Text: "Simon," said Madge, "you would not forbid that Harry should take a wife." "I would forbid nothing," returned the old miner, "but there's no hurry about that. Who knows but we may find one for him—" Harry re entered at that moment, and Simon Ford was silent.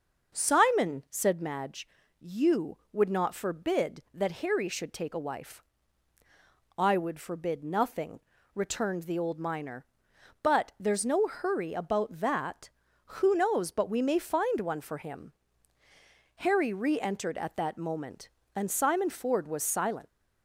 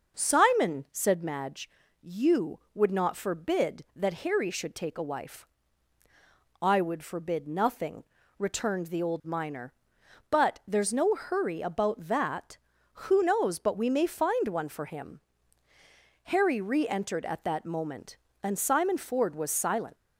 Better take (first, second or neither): neither